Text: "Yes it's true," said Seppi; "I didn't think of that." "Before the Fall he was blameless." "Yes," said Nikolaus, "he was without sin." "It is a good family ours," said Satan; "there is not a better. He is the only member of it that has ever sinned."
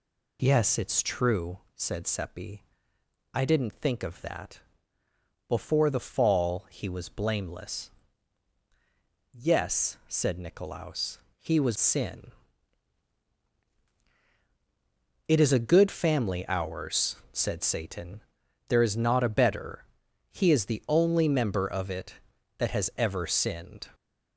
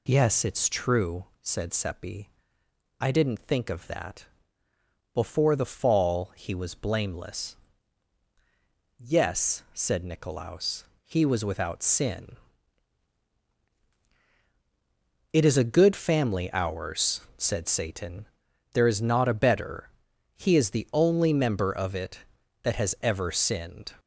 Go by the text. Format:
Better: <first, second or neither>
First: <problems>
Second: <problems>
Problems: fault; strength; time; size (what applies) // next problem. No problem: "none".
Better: second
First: skips "without"; at 11.7 s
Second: none